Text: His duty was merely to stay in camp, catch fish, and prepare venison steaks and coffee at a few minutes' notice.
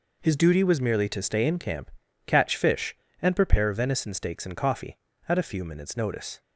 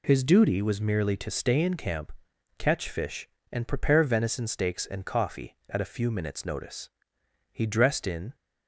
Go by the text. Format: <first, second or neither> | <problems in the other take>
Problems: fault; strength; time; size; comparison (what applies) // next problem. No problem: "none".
first | goes on to say "He dressed in"; noticeable; from 7.5 s on; 0.84 s long